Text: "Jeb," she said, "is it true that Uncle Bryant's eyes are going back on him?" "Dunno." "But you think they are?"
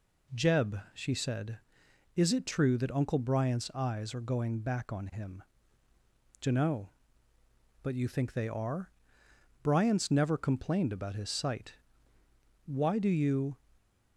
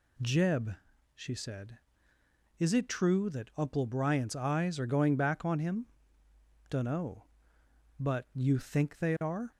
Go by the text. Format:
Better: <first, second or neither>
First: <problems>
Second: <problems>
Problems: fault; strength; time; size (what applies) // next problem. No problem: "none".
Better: second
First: goes on to say "Bryant's never complained about his sight Why do you"; strong; from 9.6 s on; 3.9 s long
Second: none